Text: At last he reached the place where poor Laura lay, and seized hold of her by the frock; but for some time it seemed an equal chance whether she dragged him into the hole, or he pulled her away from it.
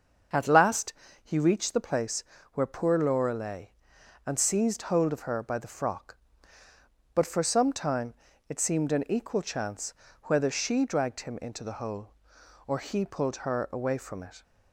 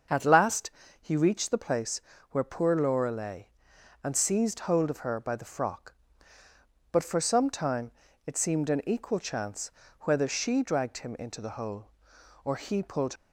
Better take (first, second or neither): first